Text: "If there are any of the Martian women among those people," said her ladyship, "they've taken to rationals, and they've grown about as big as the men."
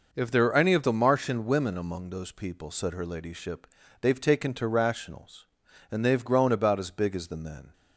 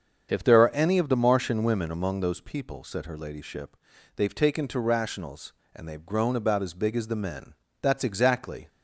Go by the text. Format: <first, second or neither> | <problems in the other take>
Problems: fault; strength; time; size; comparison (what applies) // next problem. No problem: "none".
first | starts louder than the rest; until 1.3 s; 7 dB // goes on to say "That's exactly"; noticeable; from 7.8 s on; 0.86 s long